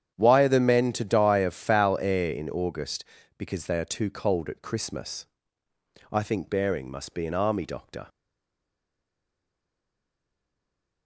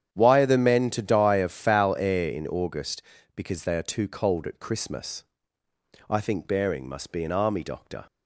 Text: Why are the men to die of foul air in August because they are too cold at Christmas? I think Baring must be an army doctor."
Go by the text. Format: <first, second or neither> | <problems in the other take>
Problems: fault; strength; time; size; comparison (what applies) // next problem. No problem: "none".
second | starts louder than the rest; strong; until 1.1 s; 9 dB; strong in the second // stays silent after the last word; strong; from 8.0 s on; 3.0 s long